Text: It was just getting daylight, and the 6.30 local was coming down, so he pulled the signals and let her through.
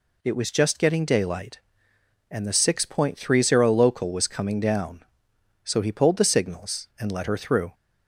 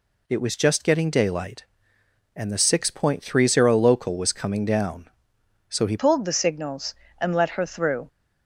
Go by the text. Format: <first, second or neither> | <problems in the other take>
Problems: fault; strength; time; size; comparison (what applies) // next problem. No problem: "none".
first | changes voice at "pulled"; from 5.9 s on; 2.1 s long